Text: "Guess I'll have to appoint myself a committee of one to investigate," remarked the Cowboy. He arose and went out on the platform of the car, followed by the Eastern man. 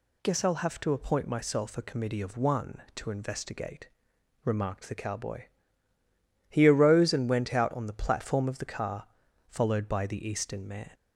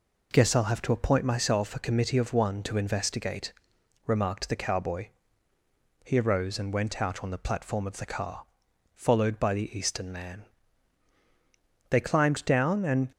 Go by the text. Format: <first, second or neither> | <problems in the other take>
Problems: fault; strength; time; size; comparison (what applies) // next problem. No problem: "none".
first | goes on to say "They climbed down and"; noticeable; from 11.8 s on; 1.2 s long